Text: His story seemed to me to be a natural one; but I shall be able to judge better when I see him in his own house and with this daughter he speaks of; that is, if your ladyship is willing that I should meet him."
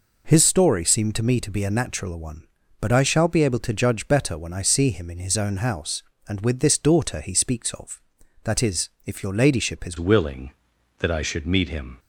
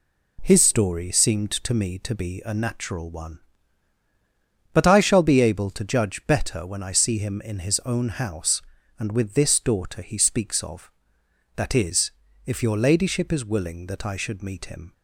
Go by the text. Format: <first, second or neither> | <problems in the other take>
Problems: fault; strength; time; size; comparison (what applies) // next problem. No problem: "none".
second | changes voice at "willing"; from 9.9 s on; 2.0 s long